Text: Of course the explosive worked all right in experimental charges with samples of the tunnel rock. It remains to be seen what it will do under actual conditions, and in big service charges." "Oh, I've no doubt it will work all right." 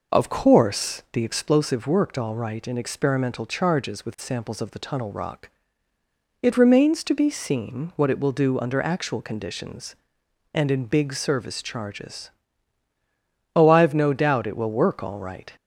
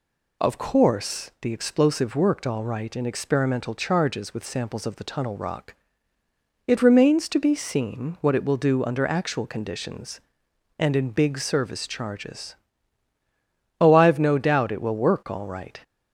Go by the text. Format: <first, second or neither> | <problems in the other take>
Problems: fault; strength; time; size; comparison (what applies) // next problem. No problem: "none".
second | starts louder than the rest; noticeable; until 1.5 s; 5 dB